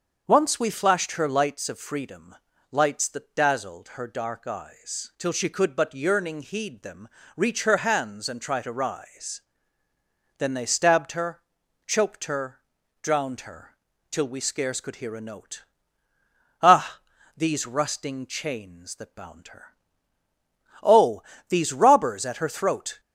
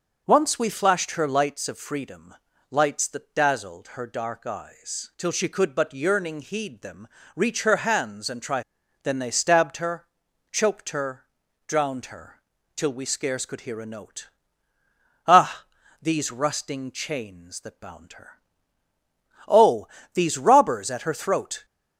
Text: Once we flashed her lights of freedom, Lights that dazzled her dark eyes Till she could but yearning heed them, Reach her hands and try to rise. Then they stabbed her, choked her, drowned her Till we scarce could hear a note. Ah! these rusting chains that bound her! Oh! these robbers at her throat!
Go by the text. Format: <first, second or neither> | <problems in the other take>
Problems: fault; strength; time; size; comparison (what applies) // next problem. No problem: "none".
first | starts louder than the rest; until 1.2 s; 6 dB; also in the first // skips "to rise"; at 8.8 s // pauses between "her" and "Till"; slight; at 12.4 s; 0.34 s long; slight in the first